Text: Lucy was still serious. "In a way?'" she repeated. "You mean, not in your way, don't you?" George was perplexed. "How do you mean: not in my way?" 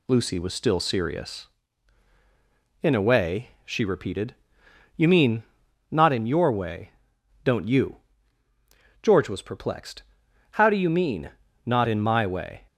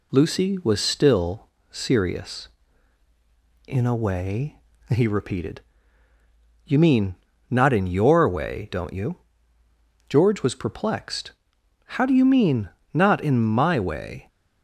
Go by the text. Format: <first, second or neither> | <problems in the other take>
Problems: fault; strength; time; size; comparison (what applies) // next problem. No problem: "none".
first | pauses between "still" and "serious"; slight; at 1.4 s; 0.20 s long // says "he" for "she"; at 4.8 s